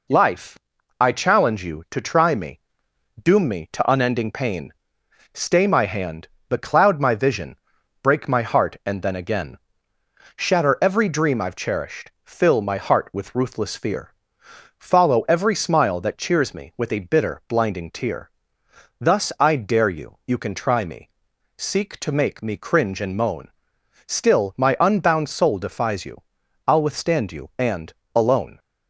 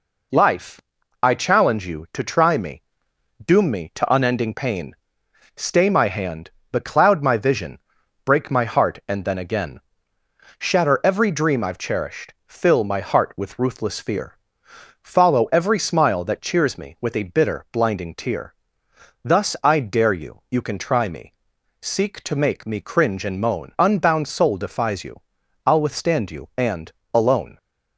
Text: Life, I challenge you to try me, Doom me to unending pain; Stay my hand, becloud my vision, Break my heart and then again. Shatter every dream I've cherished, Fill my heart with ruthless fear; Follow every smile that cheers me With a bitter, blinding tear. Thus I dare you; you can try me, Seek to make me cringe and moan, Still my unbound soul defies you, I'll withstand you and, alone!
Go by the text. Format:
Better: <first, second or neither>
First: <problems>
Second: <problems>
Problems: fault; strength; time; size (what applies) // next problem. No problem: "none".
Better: first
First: none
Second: skips "Still my"; at 23.7 s